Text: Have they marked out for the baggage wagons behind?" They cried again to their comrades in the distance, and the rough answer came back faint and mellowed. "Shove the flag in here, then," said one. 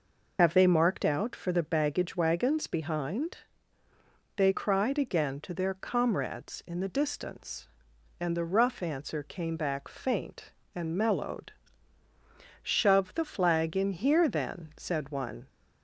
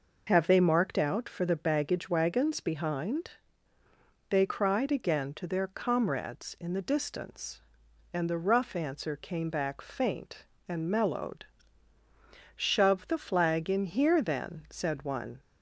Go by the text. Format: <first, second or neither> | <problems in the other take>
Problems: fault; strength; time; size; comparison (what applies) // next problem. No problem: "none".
second | loses the start of "Have"; at 0.3 s; 55 ms